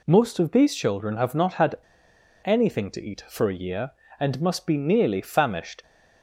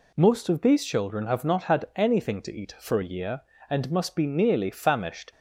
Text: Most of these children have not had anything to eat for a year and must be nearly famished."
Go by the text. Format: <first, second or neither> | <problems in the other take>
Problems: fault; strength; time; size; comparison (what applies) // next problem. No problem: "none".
second | pauses between "had" and "anything"; noticeable; at 1.7 s; 0.68 s long